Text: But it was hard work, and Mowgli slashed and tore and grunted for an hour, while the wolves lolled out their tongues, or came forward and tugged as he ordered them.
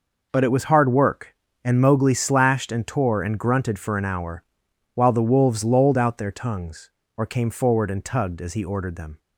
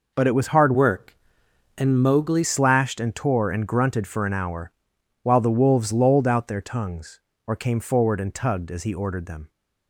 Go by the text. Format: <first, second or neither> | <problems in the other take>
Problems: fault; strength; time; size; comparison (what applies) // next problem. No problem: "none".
first | changes voice from "work" to "Mowgli"; from 0.7 to 2.4 s; 1.7 s long